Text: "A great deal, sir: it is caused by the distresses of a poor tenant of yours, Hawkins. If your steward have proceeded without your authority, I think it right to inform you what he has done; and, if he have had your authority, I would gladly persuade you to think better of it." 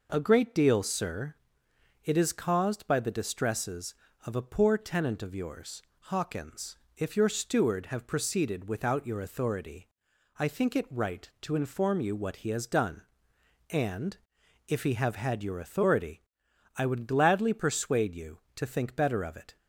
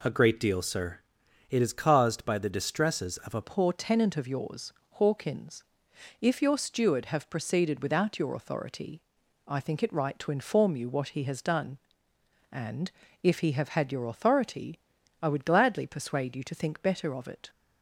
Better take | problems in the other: first | changes voice at "poor"; from 3.4 s on; 14.0 s long

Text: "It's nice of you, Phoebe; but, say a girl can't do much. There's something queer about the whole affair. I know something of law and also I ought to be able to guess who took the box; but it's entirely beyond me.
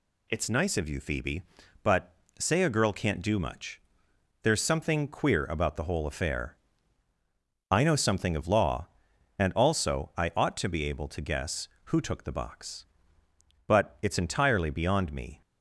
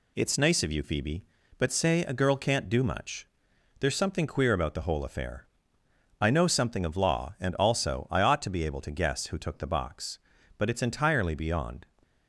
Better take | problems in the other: first | stops before "me"; at 12.0 s

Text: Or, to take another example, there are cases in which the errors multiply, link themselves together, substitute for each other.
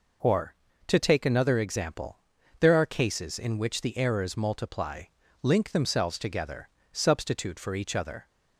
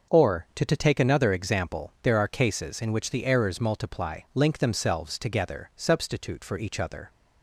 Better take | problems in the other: first | says "to" twice; at 0.6 s

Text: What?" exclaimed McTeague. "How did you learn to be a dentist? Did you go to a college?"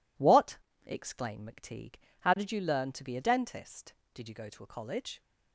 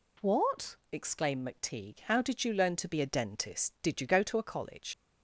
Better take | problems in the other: first | leaves "college" unfinished; at 4.9 s; 100 ms

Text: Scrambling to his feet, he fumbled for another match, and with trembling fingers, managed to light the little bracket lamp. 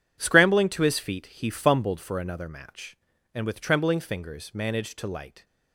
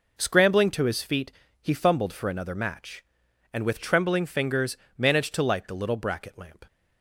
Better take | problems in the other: second | stops before "the little bracket lamp"; at 5.4 s

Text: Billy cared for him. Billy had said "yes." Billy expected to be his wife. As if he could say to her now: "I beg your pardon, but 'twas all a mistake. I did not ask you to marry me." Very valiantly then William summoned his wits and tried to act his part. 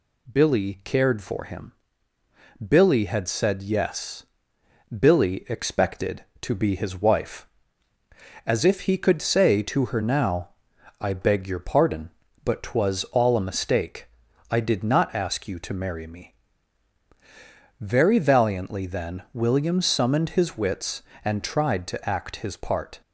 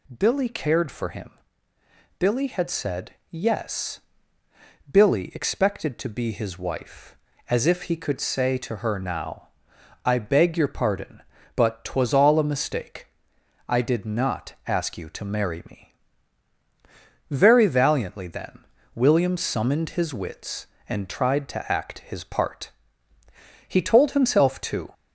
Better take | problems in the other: first | pauses between "then" and "William"; slight; at 18.6 s; 0.30 s long // goes on to say "He told himself too"; noticeable; from 23.6 s on; 1.2 s long

